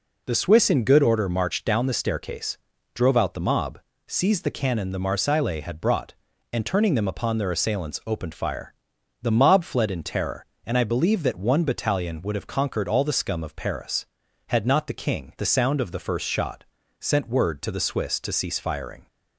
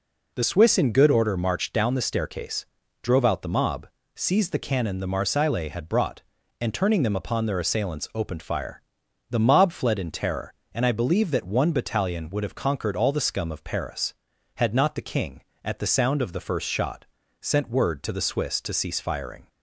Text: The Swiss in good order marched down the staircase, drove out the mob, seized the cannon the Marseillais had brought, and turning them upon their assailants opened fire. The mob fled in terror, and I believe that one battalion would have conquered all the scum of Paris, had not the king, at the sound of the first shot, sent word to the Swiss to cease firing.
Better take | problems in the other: second | skips "at"; at 15.3 s

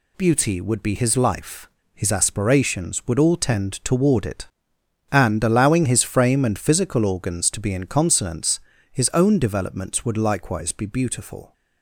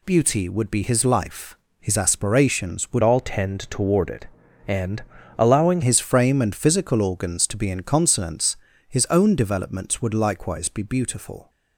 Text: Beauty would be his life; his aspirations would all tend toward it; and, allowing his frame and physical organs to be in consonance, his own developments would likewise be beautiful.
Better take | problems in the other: first | changes voice from "all" to "allowing"; from 3.0 to 5.8 s; 2.8 s long

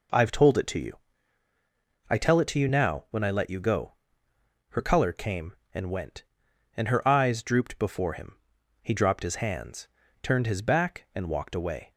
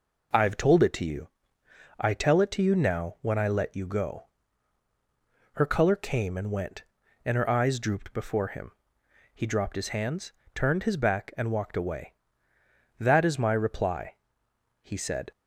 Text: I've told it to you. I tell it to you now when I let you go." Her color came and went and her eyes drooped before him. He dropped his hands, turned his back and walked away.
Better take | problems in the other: first | goes on to say "That is my reply he said"; strong; from 12.9 s on; 2.3 s long

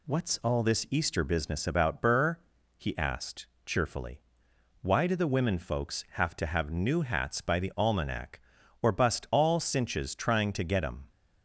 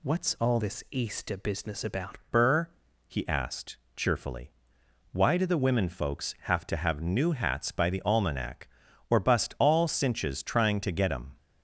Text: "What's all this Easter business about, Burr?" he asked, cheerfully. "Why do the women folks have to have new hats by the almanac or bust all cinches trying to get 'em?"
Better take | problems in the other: first | changes voice from "this" to "about"; from 0.5 to 2.1 s; 1.6 s long

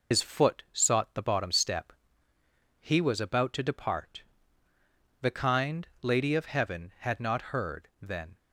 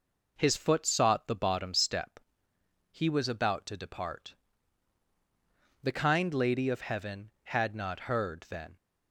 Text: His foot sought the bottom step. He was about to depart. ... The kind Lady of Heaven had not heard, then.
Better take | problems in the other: second | loses the start of "His"; at 0.1 s; 95 ms // pauses between "kind" and "Lady"; slight; at 5.8 s; 0.18 s long

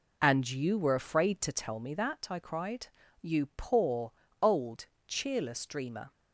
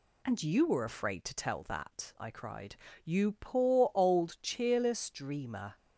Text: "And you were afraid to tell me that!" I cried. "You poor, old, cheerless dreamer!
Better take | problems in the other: first | skips "me"; at 1.6 s

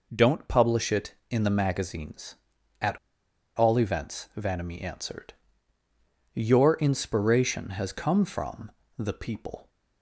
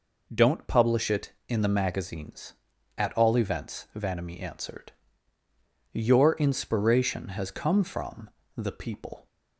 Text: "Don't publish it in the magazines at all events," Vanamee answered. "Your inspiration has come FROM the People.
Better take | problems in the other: second | pauses between "at" and "all"; noticeable; at 2.9 s; 0.61 s long // pauses between "FROM" and "the"; slight; at 8.7 s; 0.26 s long; slight in the second

